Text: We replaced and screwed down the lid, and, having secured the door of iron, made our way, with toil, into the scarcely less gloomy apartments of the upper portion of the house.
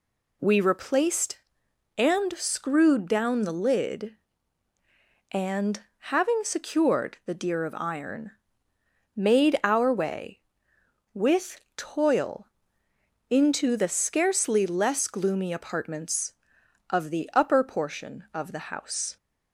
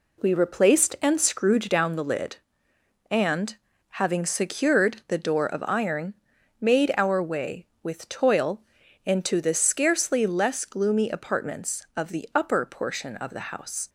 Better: second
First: says "deer" for "door"; at 7.3 s // pauses between "with" and "toil"; slight; at 11.6 s; 0.16 s long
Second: none

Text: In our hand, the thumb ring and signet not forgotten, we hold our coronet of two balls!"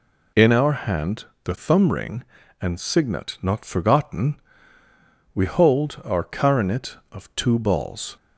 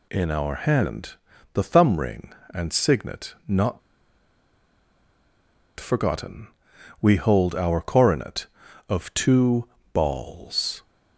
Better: first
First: none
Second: pauses between "not" and "forgotten"; strong; at 3.7 s; 1.9 s long // pauses between "two" and "balls"; slight; at 9.6 s; 0.28 s long

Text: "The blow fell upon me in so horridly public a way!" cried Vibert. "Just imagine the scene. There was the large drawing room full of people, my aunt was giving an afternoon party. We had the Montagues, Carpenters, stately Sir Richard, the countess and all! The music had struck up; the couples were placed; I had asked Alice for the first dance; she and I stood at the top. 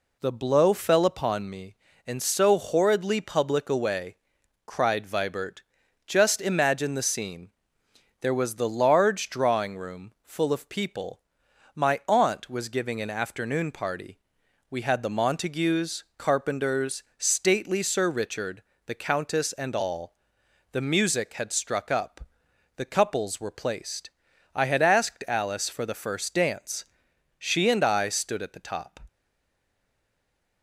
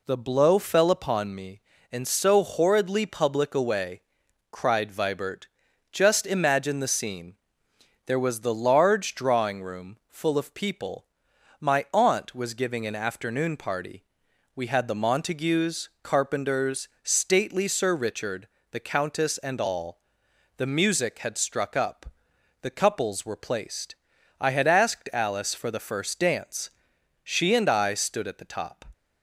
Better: second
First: stays silent after the last word; noticeable; from 29.0 s on; 1.6 s long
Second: none

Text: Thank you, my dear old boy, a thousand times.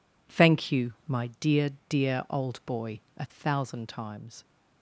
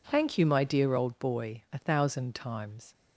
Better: second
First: says "dear" twice; at 1.8 s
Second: none

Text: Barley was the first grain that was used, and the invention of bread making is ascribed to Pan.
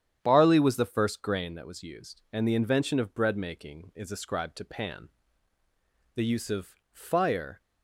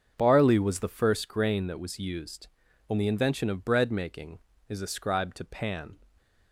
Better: second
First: starts louder than the rest; strong; until 1.2 s; 9.5 dB // goes on to say "The use of fire"; from 6.1 s on; 1.4 s long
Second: starts louder than the rest; until 1.1 s; 7 dB

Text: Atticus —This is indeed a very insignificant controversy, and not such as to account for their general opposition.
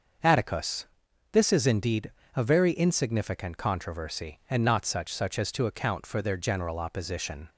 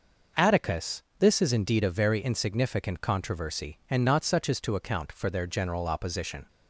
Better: second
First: starts louder than the rest; until 1.6 s; 6.5 dB // pauses between "indeed" and "a"; slight; at 2.1 s; 0.24 s long // says "such" twice; at 5.1 s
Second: none

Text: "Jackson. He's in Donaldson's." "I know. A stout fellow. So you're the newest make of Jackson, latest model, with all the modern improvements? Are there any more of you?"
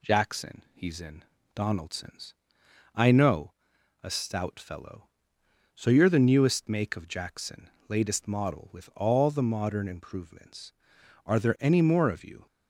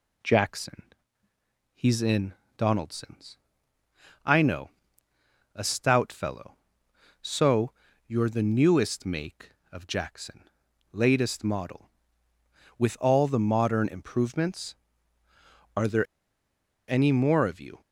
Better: first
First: pauses between "in" and "Donaldson's"; slight; at 1.2 s; 0.32 s long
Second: pauses between "in" and "Donaldson's"; slight; at 2.3 s; 0.24 s long // pauses between "So" and "you're"; slight; at 7.7 s; 0.34 s long // pauses between "there" and "any"; noticeable; at 16.0 s; 0.82 s long

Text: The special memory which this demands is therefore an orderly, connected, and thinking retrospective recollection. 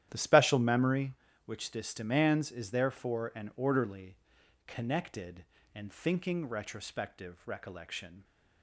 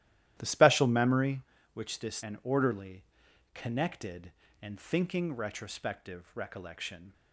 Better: first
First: starts louder than the rest; strong; until 1.1 s; 11.5 dB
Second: starts louder than the rest; strong; until 1.3 s; 13 dB // skips "demands is therefore"; at 2.2 s

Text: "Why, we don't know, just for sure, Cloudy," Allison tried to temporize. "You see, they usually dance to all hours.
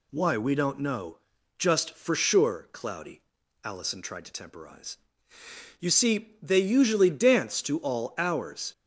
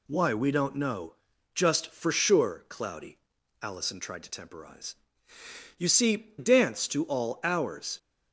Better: first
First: none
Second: skips "they usually"; at 6.3 s

